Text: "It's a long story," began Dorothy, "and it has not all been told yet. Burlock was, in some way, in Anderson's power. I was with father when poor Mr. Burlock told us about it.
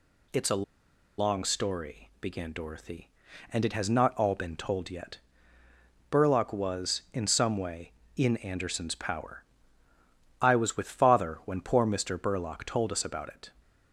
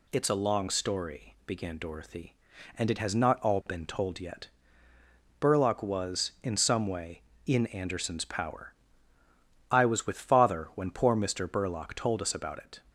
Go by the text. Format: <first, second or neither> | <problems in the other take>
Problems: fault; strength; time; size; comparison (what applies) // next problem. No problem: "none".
second | pauses between "a" and "long"; noticeable; at 0.6 s; 0.55 s long